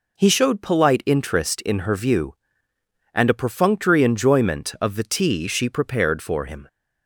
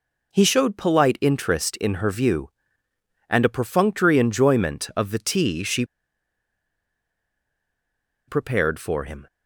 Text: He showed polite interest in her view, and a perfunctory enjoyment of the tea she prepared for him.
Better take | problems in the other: first | pauses between "she" and "prepared"; strong; at 5.8 s; 2.4 s long

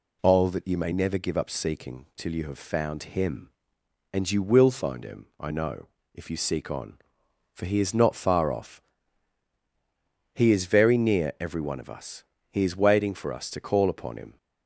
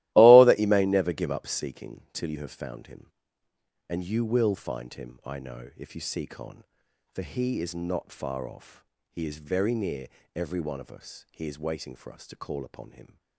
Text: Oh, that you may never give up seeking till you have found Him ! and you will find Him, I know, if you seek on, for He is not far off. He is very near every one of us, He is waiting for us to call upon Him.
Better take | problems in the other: first | starts louder than the rest; strong; until 1.7 s; 16 dB // pauses between "near" and "every"; slight; at 10.0 s; 0.28 s long

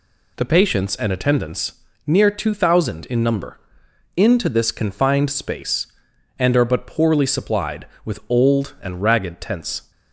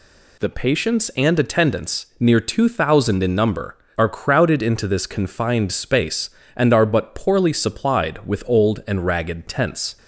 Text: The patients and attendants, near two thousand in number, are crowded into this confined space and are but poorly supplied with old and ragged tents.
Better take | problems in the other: second | skips "are crowded"; at 3.8 s

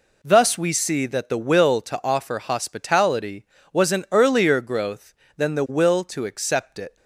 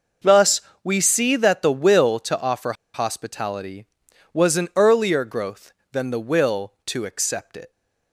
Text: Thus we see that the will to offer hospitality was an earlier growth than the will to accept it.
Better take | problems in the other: first | pauses between "Thus" and "we"; slight; at 0.6 s; 0.22 s long // pauses between "offer" and "hospitality"; slight; at 2.7 s; 0.21 s long

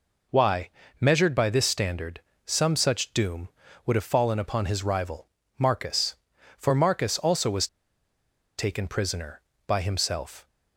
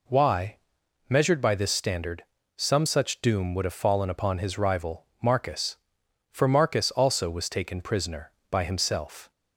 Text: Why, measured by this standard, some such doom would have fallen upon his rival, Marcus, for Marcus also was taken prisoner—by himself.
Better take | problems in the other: second | pauses between "was" and "taken"; noticeable; at 7.6 s; 0.91 s long

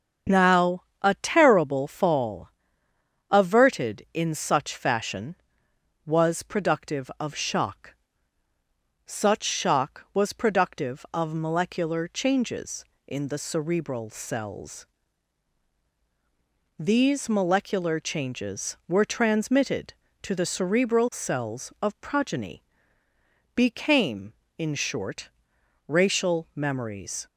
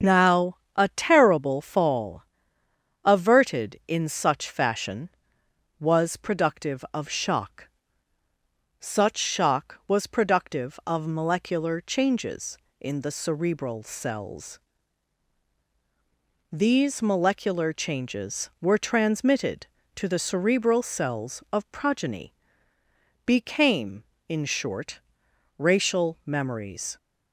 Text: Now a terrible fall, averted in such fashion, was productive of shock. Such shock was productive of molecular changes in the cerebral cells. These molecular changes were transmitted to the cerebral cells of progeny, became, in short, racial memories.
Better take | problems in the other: neither | starts louder than the rest; strong; the same in both // pauses between "Now" and "a"; slight; the same in both

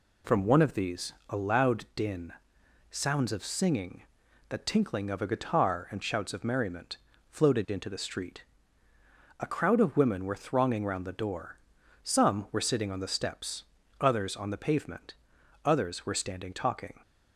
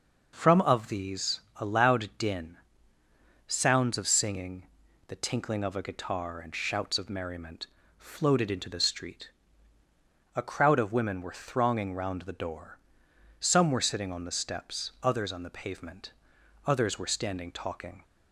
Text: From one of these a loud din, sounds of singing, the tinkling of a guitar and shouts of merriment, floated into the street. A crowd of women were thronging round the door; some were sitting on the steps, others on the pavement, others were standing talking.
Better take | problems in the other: first | skips "one"; at 0.6 s // pauses between "these" and "a"; slight; at 1.4 s; 0.16 s long; slight in the first

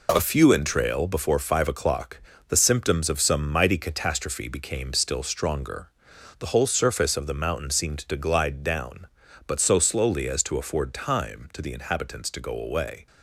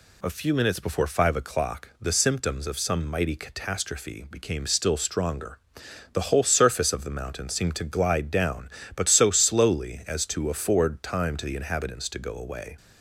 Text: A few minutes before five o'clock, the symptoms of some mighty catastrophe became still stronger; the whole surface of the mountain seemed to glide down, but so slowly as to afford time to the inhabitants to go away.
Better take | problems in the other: second | says "entrail" for "minutes"; at 0.5 s

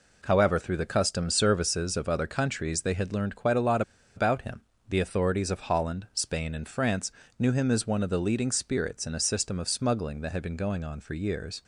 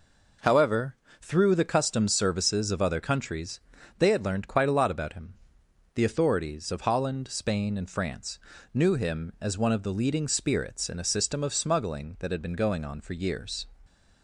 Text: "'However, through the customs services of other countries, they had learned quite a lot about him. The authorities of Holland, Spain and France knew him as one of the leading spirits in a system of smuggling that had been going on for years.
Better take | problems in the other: second | pauses between "lot" and "about"; slight; at 3.8 s; 0.34 s long // pauses between "France" and "knew"; slight; at 7.1 s; 0.28 s long; slight in the second

